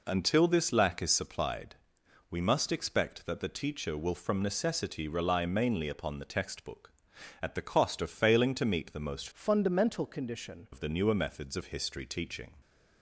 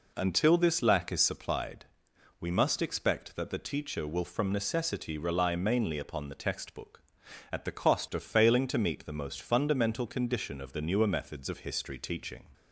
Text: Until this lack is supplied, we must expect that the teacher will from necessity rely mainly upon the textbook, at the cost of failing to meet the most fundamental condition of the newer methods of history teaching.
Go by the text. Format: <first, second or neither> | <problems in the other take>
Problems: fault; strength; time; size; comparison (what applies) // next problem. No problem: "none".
second | changes voice from "fundamental" to "condition"; from 9.3 to 10.6 s; 1.3 s long